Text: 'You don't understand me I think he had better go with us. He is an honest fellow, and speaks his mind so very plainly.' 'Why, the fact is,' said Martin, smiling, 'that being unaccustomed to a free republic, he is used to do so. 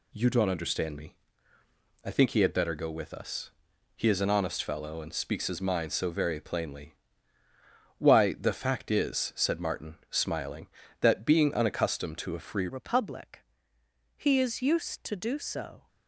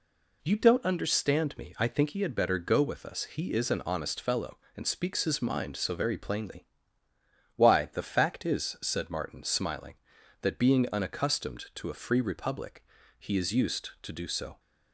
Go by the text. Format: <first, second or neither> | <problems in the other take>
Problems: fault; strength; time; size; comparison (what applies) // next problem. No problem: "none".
second | pauses between "me" and "I"; noticeable; at 1.1 s; 0.88 s long // changes voice at "republic"; from 12.6 s on; 3.2 s long